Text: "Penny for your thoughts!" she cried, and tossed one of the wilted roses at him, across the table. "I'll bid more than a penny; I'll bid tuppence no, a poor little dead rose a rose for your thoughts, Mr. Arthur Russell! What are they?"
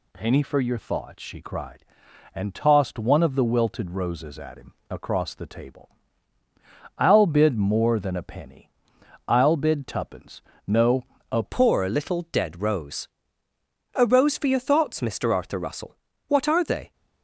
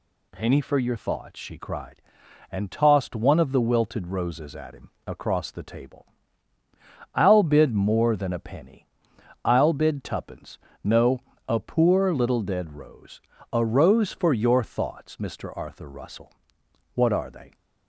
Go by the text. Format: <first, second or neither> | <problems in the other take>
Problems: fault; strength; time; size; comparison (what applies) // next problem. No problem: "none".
second | pauses between "tuppence" and "no"; slight; at 10.4 s; 0.26 s long; slight in the second // changes voice at "poor"; from 11.4 s on; 5.5 s long // pauses between "rose" and "a"; noticeable; at 13.0 s; 0.86 s long; slight in the second